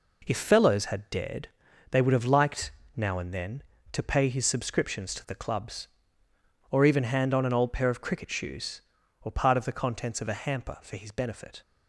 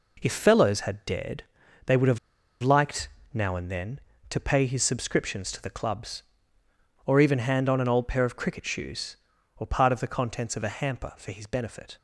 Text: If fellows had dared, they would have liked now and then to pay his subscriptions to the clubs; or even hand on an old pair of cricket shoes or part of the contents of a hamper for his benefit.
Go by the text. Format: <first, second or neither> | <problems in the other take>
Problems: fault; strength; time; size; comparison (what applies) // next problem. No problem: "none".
first | pauses between "have" and "liked"; at 2.1 s; 0.43 s long // pauses between "liked" and "now"; slight; at 3.0 s; 0.24 s long; slight in the first